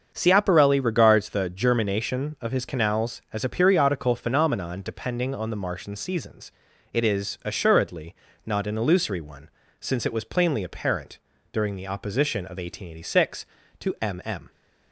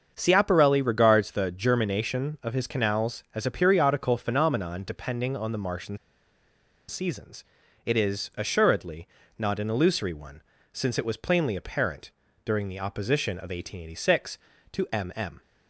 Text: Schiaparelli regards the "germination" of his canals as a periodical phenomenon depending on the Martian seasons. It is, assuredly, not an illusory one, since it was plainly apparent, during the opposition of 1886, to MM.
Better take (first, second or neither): first